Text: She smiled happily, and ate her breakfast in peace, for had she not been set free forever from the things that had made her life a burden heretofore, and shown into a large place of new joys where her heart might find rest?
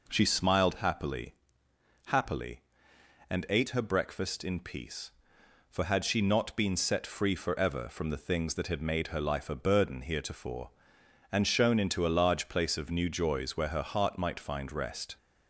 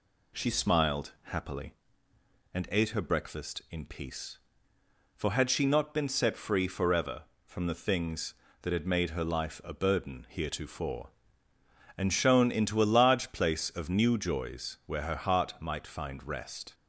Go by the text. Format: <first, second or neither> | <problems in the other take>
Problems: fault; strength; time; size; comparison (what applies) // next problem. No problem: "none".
second | says "happily" twice; at 2.1 s